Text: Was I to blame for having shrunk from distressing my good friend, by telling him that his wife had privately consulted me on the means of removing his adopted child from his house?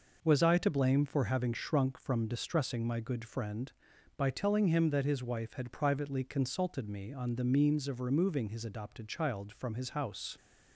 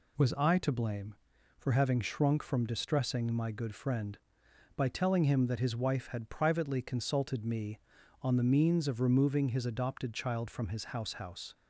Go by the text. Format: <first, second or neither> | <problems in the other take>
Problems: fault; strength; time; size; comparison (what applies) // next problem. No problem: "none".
first | says "house" twice; at 11.1 s